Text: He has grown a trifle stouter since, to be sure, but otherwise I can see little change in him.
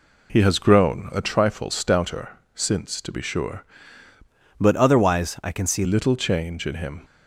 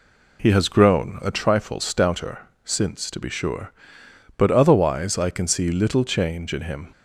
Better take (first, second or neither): second